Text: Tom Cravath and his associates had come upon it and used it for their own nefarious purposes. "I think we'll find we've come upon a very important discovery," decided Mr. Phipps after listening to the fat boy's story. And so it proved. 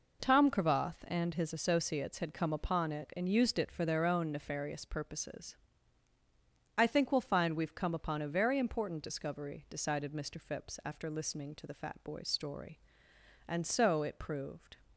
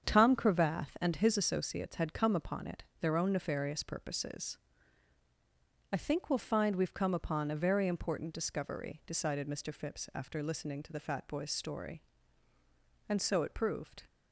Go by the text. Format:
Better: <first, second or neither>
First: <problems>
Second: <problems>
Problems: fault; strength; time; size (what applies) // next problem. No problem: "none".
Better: first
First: none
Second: starts louder than the rest; strong; until 1.1 s; 7.5 dB // skips "and used it for"; at 2.9 s